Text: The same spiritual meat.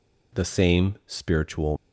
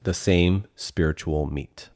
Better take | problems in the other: second | stops before "meat"; at 1.7 s

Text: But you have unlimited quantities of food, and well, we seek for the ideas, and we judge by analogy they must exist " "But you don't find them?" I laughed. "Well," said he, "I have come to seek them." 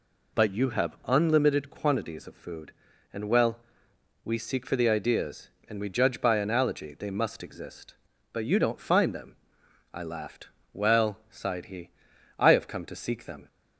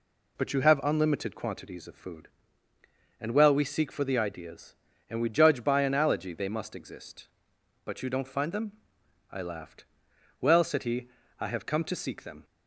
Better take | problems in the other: second | says "sighed" for "said"; at 11.2 s

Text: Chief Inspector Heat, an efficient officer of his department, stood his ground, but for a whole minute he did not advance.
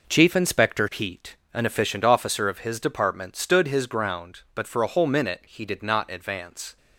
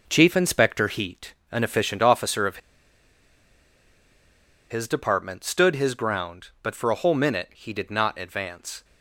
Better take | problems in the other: first | pauses between "of" and "his"; strong; at 2.5 s; 2.1 s long

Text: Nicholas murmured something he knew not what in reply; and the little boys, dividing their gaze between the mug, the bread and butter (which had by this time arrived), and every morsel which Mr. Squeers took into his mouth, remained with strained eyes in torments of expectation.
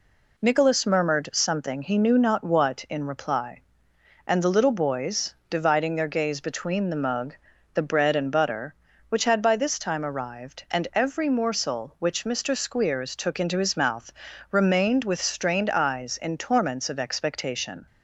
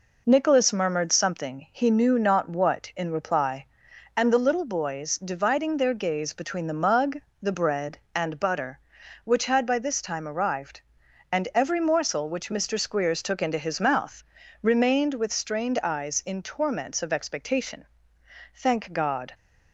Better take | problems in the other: first | goes on to say "Thank God"; noticeable; from 18.5 s on; 0.80 s long

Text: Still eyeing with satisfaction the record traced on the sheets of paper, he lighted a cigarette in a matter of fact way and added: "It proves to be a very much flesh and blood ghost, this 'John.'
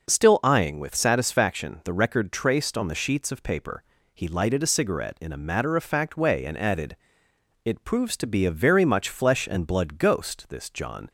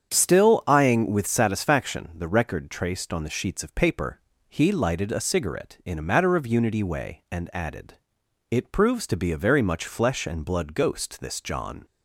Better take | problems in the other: first | starts louder than the rest; strong; until 1.1 s; 8 dB // says "unity" for "fact"; at 6.4 s

